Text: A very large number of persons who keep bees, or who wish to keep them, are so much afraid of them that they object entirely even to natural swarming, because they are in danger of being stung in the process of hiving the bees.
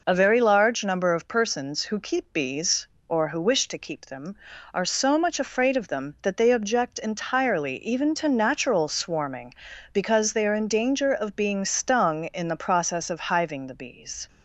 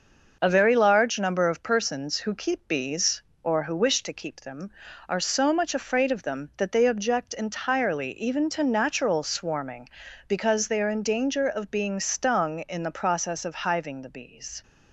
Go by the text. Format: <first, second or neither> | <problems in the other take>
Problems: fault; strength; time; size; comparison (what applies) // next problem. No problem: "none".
first | gets quieter; throughout; 4 dB